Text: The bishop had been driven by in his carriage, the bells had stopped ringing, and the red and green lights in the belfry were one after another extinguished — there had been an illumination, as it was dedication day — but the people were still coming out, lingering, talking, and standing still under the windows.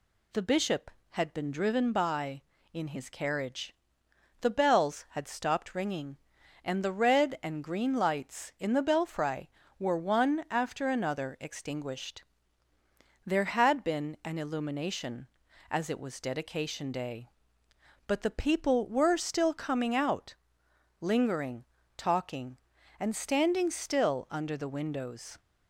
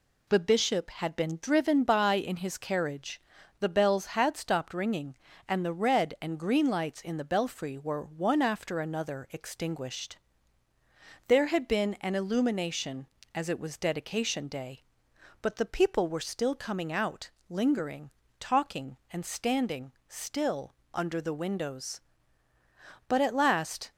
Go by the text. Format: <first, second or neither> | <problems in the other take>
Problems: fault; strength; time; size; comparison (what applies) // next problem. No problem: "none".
first | pauses between "standing" and "still"; slight; at 19.9 s; 0.16 s long // pauses between "still" and "under"; slight; at 20.7 s; 0.22 s long // goes on to say "But at last"; noticeable; from 23.0 s on; 0.82 s long